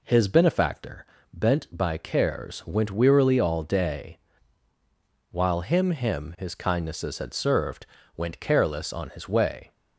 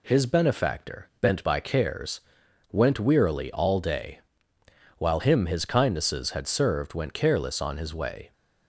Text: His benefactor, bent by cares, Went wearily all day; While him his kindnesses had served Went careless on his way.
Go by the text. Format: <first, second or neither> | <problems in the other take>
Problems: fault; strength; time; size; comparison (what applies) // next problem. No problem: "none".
second | says "him" twice; at 5.9 s // pauses between "served" and "Went"; slight; at 7.8 s; 0.30 s long